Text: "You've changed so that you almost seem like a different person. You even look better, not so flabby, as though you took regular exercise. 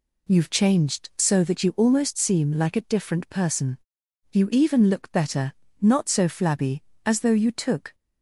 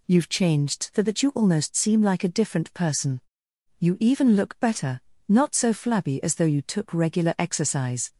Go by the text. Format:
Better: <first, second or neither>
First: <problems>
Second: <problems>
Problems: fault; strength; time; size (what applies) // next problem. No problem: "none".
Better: second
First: stops before "regular exercise"; at 7.9 s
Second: none